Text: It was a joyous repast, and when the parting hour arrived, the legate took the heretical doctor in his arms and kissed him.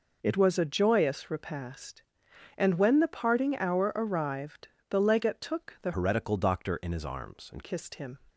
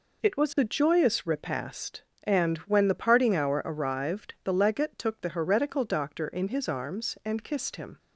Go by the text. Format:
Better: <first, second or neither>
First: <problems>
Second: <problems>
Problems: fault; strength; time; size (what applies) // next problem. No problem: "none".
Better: second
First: changes voice from "heretical" to "and"; from 5.9 to 7.6 s; 1.7 s long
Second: none